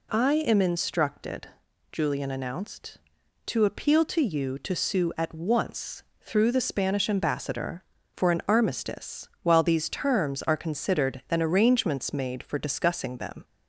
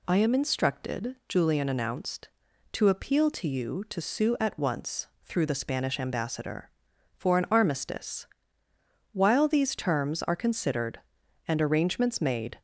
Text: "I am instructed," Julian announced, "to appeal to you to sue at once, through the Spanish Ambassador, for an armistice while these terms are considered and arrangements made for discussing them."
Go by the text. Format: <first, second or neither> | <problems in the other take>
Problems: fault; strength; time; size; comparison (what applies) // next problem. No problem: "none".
first | pauses between "armistice" and "while"; noticeable; at 8.2 s; 0.86 s long; slight in the first // stops before "for discussing them"; at 12.5 s